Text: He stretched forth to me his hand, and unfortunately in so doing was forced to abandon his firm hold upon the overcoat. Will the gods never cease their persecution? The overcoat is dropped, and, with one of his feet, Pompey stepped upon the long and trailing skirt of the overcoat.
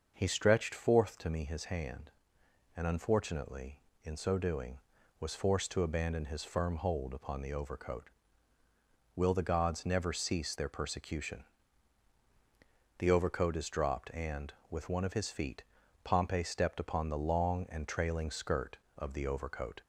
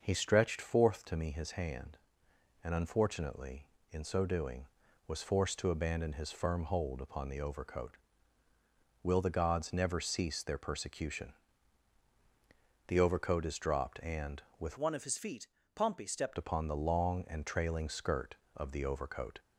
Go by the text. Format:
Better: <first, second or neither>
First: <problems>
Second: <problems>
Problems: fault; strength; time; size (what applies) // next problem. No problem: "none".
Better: first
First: starts louder than the rest; until 1.1 s; 6 dB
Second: starts louder than the rest; until 1.0 s; 6 dB // changes voice from "one" to "stepped"; from 14.7 to 16.3 s; 1.6 s long